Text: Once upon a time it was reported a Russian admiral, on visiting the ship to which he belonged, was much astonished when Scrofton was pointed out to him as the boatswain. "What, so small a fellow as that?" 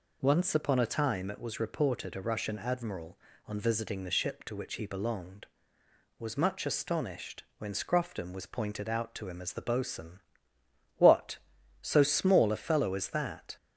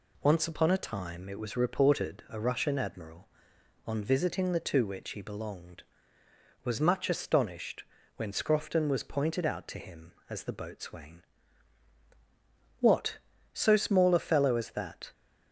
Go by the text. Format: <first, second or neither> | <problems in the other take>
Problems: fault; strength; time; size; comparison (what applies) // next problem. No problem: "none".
first | skips "ship"; at 4.5 s // pauses between "astonished" and "when"; slight; at 7.8 s; 0.32 s long; slight in the first